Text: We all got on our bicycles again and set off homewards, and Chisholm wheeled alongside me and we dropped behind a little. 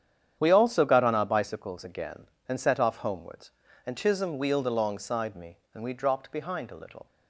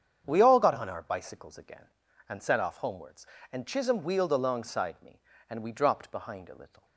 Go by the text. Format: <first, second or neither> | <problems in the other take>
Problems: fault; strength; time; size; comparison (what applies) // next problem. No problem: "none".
second | starts louder than the rest; strong; until 1.4 s; 9 dB; strong in the second // says "also" for "all"; at 0.5 s